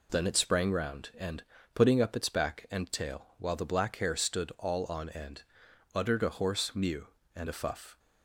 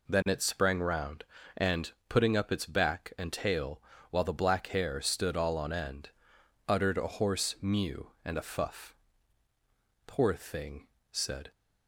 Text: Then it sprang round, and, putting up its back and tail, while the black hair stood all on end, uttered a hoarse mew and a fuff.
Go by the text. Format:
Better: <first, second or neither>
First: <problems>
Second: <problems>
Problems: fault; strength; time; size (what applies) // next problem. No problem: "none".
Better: first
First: none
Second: goes on to say "Poor thing said"; from 10.0 s on; 1.4 s long